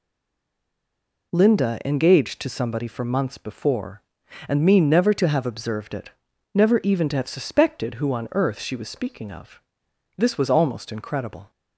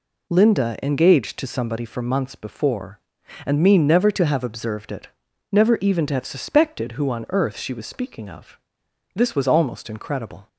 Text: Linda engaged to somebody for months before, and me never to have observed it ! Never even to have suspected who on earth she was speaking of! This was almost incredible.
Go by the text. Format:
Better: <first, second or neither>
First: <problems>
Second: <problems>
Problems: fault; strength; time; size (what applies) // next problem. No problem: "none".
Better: second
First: stays silent before the first word; noticeable; until 1.3 s; 1.3 s long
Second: none